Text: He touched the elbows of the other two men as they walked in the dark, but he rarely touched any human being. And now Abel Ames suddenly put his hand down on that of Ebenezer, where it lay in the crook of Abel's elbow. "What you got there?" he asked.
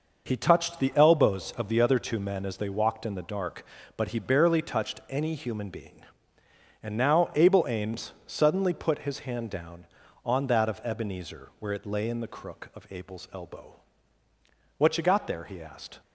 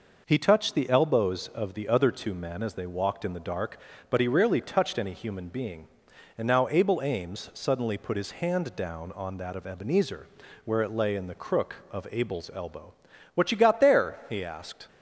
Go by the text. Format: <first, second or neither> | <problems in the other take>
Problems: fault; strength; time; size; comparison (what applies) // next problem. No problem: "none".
second | says "barely" for "rarely"; at 4.1 s // pauses between "Ames" and "suddenly"; slight; at 8.1 s; 0.16 s long